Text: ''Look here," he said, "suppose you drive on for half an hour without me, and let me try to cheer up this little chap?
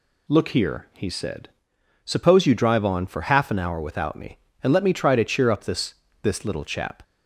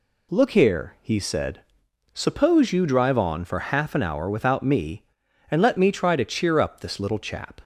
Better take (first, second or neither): second